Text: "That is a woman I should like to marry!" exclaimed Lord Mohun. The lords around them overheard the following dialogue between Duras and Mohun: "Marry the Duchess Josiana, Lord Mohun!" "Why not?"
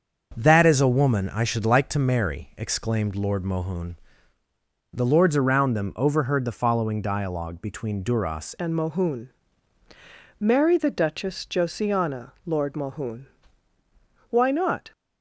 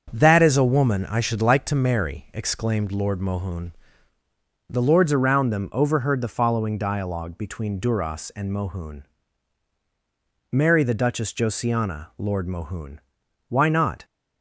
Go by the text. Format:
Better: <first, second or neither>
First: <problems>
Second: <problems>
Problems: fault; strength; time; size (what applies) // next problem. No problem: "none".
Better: second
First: starts louder than the rest; until 1.3 s; 7 dB // changes voice at "and"; from 8.5 s on; 6.4 s long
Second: starts louder than the rest; strong; until 1.1 s; 7 dB